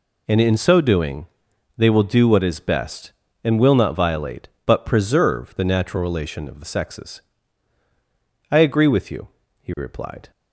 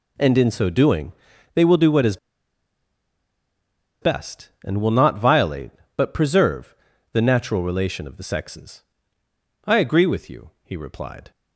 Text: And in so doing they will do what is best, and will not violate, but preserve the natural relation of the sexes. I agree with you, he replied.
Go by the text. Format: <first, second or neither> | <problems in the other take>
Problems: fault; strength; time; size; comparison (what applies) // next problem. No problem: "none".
first | pauses between "doing" and "they"; at 1.1 s; 0.42 s long; noticeable in the first // pauses between "is" and "best"; strong; at 2.1 s; 1.8 s long // pauses between "preserve" and "the"; at 6.7 s; 0.38 s long